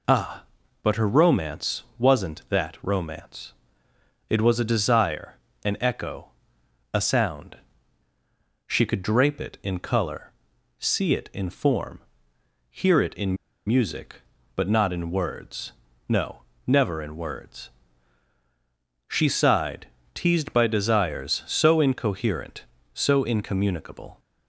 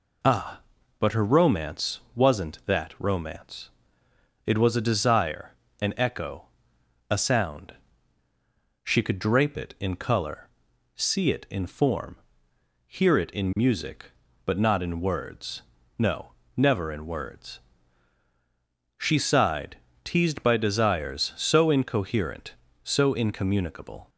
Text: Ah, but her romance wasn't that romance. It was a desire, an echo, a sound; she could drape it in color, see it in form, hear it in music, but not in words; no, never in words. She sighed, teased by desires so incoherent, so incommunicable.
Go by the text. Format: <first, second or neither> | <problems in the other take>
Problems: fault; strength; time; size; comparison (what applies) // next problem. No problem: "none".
second | pauses between "romance" and "wasn't"; slight; at 1.8 s; 0.16 s long; slight in the second // pauses between "in" and "music"; slight; at 13.3 s; 0.30 s long